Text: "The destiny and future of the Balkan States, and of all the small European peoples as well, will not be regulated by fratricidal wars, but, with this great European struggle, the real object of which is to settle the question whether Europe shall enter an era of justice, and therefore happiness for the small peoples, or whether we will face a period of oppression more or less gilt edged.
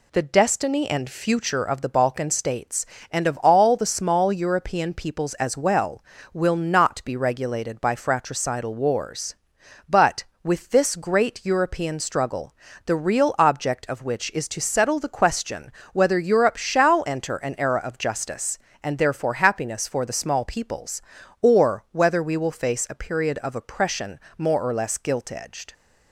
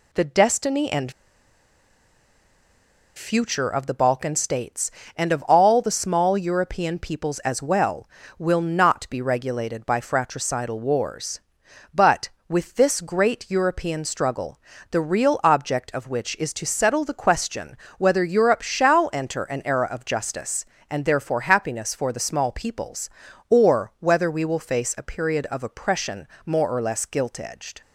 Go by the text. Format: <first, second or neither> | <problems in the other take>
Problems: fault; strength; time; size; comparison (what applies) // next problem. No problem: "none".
first | pauses between "and" and "future"; strong; at 1.1 s; 2.0 s long // pauses between "question" and "whether"; slight; at 17.7 s; 0.20 s long; slight in the first // pauses between "oppression" and "more"; slight; at 26.2 s; 0.18 s long; slight in the first